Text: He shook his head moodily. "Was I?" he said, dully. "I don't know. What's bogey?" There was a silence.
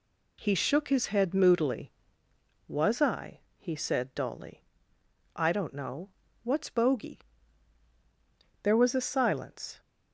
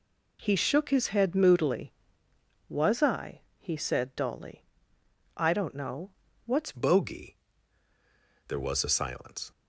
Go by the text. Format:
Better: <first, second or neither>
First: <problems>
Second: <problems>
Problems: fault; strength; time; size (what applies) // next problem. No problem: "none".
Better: first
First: none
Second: changes voice at "bogey"; from 6.7 s on; 2.8 s long